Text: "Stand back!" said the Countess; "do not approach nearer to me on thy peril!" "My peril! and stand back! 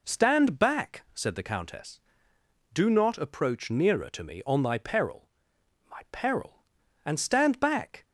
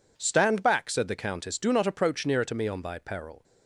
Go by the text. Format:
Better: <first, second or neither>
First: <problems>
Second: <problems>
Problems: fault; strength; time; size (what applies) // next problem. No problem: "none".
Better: first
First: none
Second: stops before "My peril and stand back"; at 3.4 s